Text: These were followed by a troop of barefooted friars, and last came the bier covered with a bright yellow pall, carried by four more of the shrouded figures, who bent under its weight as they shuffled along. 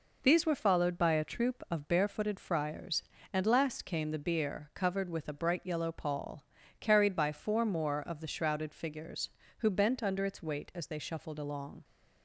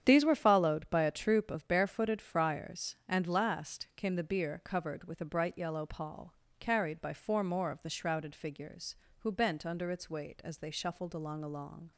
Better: first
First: none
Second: starts louder than the rest; strong; until 1.0 s; 9 dB // says "along" twice; at 11.4 s

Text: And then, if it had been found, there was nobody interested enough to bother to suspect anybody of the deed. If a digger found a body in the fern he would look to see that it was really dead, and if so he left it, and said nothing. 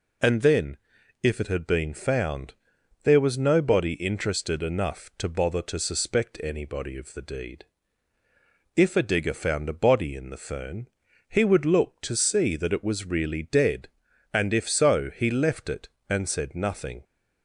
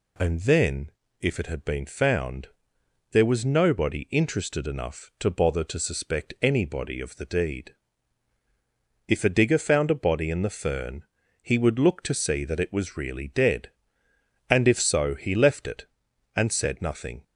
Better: neither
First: pauses between "fern" and "he"; at 10.8 s; 0.38 s long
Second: pauses between "fern" and "he"; slight; at 11.0 s; 0.36 s long

